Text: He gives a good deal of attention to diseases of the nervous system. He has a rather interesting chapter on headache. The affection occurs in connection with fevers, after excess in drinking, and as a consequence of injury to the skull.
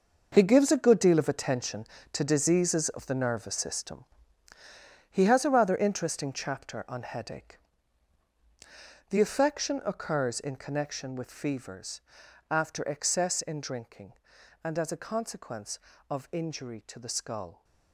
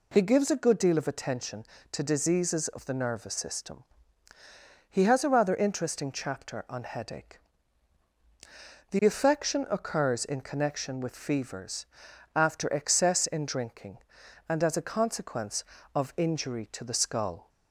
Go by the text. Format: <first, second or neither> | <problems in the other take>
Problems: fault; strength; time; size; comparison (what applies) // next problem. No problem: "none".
second | gets quieter; strong; throughout; 12 dB